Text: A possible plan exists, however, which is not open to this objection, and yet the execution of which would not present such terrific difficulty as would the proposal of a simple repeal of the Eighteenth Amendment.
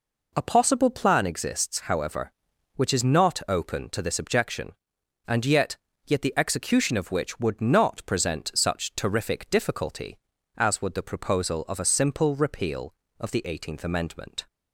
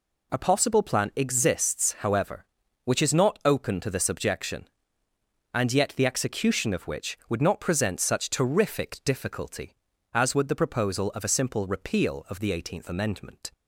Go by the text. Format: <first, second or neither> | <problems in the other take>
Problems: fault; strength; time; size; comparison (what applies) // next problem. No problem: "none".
second | says "yet" twice; at 6.0 s